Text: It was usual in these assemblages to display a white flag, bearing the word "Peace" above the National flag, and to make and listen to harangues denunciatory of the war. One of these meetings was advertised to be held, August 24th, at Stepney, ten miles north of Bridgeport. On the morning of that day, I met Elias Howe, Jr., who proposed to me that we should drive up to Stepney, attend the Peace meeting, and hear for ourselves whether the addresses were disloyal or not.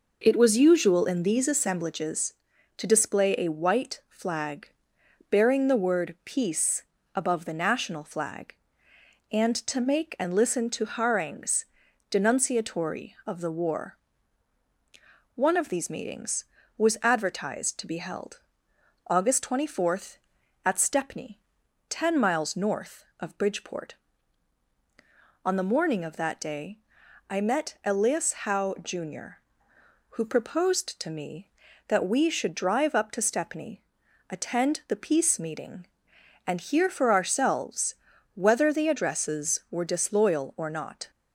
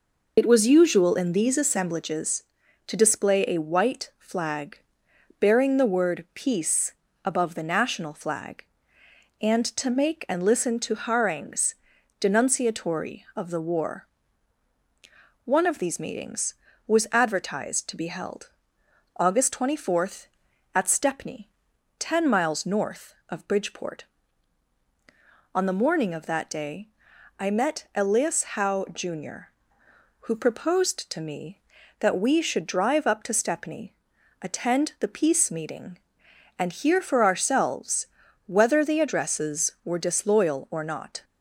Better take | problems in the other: first | loses the start of "It"; at 0.3 s; 65 ms // pauses between "Peace" and "above"; slight; at 6.9 s; 0.28 s long; slight in the first // pauses between "harangues" and "denunciatory"; at 11.7 s; 0.44 s long; also in the first // pauses between "ourselves" and "whether"; at 38.0 s; 0.40 s long; also in the first

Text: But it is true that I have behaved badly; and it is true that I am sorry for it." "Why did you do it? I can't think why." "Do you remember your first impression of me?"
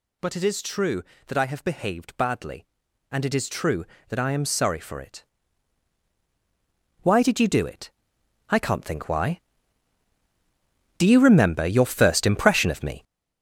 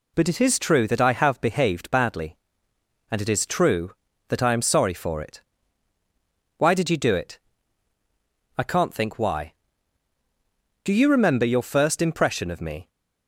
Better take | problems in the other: second | gets louder; strong; throughout; 8 dB

